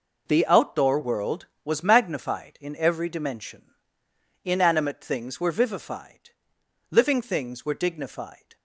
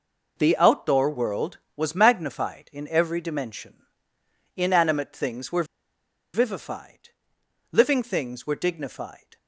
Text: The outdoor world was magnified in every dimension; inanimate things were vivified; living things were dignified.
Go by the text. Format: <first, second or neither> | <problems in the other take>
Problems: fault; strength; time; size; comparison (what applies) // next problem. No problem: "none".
first | pauses between "were" and "vivified"; noticeable; at 5.6 s; 0.70 s long